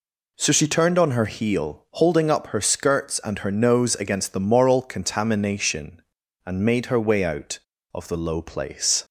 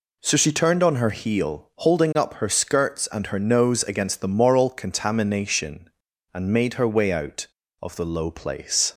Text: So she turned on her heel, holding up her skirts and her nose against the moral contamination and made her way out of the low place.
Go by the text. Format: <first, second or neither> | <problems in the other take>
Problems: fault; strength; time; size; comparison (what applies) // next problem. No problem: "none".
neither | none